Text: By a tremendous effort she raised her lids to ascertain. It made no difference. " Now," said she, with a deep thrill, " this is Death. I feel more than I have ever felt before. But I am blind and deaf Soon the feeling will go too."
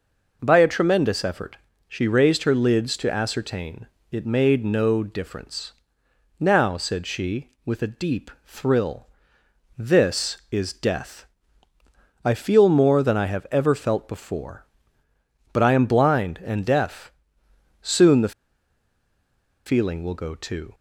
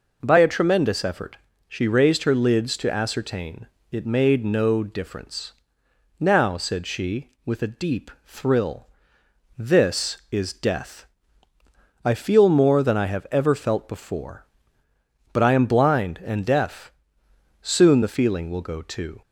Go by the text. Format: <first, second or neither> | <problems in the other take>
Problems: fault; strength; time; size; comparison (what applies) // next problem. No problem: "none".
second | starts louder than the rest; until 1.4 s; 6.5 dB // pauses between "effort" and "she"; slight; at 1.5 s; 0.28 s long; slight in the second // pauses between "deep" and "thrill"; slight; at 8.2 s; 0.16 s long; slight in the second // pauses between "deaf" and "Soon"; noticeable; at 17.1 s; 0.70 s long; noticeable in the second // pauses between "the" and "feeling"; strong; at 18.3 s; 1.3 s long